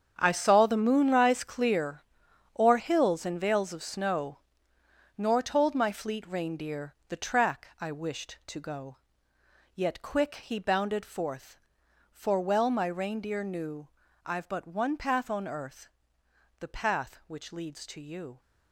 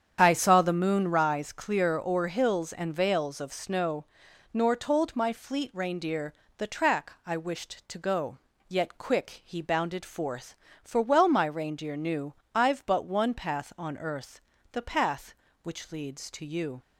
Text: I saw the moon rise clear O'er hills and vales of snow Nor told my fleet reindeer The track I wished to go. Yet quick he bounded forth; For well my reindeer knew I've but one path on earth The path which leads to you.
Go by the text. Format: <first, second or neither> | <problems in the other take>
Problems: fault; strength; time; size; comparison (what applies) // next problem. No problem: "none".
second | gets quieter; strong; throughout; 13.5 dB // starts louder than the rest; strong; until 1.1 s; 7.5 dB; strong in the second // pauses between "clear" and "O'er"; noticeable; at 2.0 s; 0.56 s long // pauses between "snow" and "Nor"; noticeable; at 4.3 s; 0.80 s long; noticeable in the second // pauses between "reindeer" and "The"; slight; at 6.9 s; 0.16 s long; slight in the second // pauses between "knew" and "I've"; slight; at 13.8 s; 0.36 s long; slight in the second // pauses between "earth" and "The"; noticeable; at 15.9 s; 0.70 s long; slight in the second